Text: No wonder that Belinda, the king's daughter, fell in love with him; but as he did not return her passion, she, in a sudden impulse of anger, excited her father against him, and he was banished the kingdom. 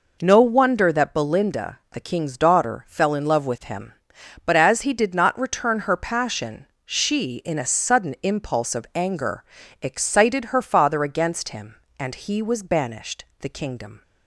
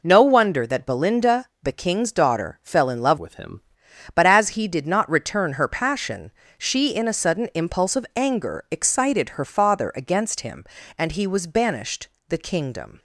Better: first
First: pauses between "banished" and "the"; slight; at 13.2 s; 0.16 s long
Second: changes voice from "with" to "him"; from 3.1 to 3.6 s; 0.5 s long // pauses between "banished" and "the"; slight; at 12.0 s; 0.18 s long

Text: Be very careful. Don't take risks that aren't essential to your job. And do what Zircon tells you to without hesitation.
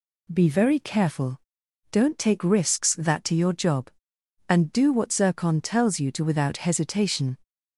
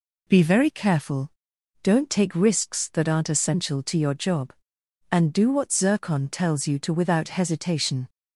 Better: second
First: skips "aren't essential"; at 3.2 s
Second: none

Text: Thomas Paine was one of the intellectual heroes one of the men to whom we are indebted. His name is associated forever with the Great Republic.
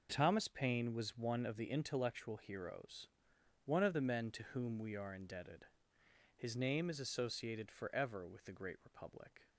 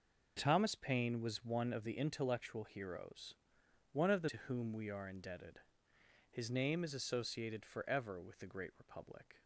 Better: first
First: pauses between "heroes" and "one"; noticeable; at 3.0 s; 0.58 s long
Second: pauses between "heroes" and "one"; noticeable; at 3.3 s; 0.58 s long // skips "men"; at 4.2 s

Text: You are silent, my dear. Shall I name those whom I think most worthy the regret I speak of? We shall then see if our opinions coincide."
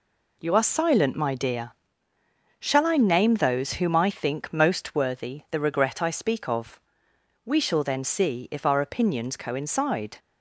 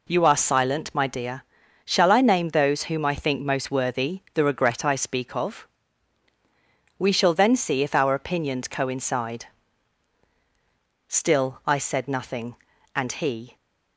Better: first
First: none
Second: goes on to say "Still I said nothing and he"; strong; from 11.0 s on; 2.4 s long

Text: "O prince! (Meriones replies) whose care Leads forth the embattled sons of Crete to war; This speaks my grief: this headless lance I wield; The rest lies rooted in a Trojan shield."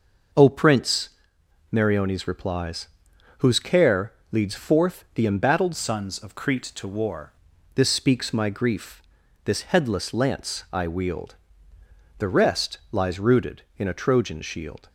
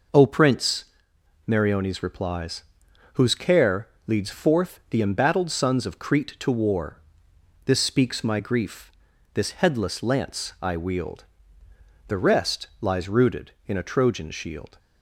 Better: second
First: pauses between "care" and "Leads"; slight; at 4.1 s; 0.18 s long // changes voice from "sons" to "war"; from 5.7 to 7.3 s; 1.6 s long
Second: pauses between "care" and "Leads"; slight; at 3.8 s; 0.18 s long

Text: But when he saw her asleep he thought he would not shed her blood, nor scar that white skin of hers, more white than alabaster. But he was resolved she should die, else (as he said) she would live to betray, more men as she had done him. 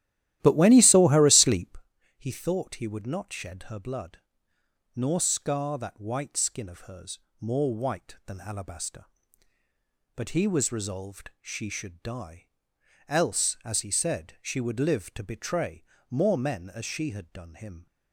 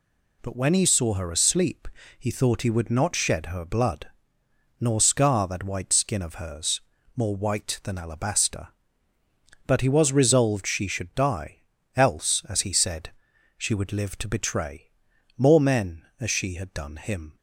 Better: second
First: starts louder than the rest; strong; until 1.8 s; 13.5 dB // pauses between "asleep" and "he"; at 1.7 s; 0.44 s long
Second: pauses between "asleep" and "he"; slight; at 1.8 s; 0.30 s long

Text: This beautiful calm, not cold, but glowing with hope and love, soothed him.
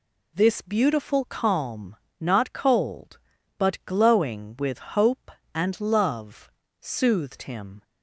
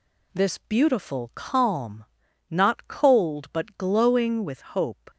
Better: first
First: none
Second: stops before "and love soothed him"; at 5.0 s

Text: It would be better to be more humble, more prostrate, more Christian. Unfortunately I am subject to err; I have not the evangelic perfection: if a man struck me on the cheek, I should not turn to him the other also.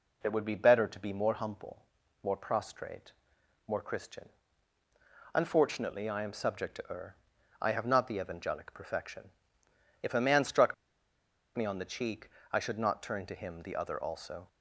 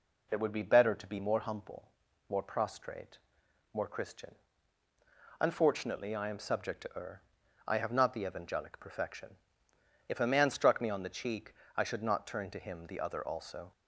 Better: second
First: pauses between "struck" and "me"; noticeable; at 10.7 s; 0.83 s long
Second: none

